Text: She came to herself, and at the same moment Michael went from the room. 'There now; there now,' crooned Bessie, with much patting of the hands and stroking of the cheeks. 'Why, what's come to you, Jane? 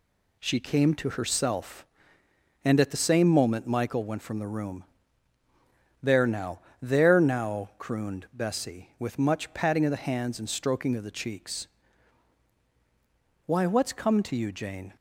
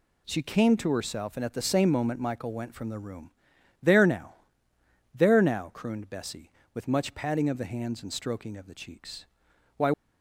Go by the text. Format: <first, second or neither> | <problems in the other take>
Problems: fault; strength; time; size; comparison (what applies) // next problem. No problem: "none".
first | stops before "what's come to you Jane"; at 9.9 s